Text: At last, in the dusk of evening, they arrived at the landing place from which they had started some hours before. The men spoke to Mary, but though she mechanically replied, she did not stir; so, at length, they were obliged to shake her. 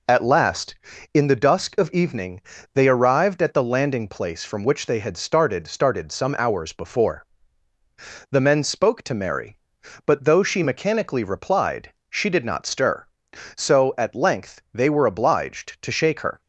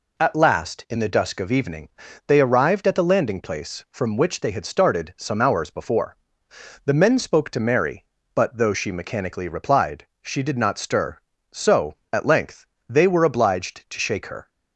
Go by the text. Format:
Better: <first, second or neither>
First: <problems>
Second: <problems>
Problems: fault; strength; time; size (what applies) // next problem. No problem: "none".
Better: second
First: says "started" twice; at 5.6 s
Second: none